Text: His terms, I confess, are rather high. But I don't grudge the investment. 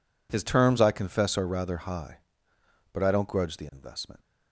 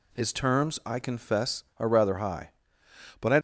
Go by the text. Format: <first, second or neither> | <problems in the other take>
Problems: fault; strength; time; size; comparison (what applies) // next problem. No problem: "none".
first | stops before "don't grudge the investment"; at 3.3 s